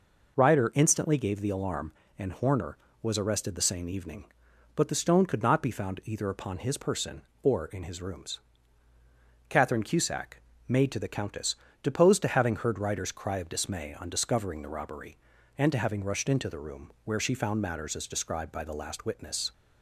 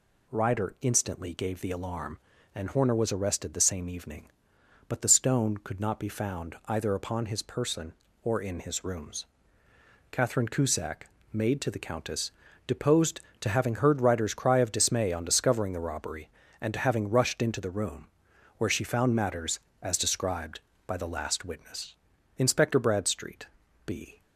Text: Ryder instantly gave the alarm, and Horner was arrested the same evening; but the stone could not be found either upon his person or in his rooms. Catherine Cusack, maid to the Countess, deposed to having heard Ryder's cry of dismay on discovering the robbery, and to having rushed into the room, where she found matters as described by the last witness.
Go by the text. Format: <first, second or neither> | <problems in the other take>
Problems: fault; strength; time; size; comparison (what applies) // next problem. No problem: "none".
first | goes on to say "Inspector Bradstreet B"; strong; from 22.3 s on; 1.8 s long